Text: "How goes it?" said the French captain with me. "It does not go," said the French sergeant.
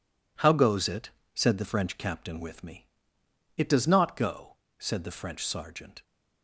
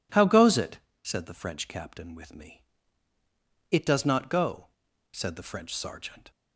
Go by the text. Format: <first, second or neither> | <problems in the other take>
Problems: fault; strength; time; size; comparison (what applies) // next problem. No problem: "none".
second | gets quieter; strong; throughout; 9 dB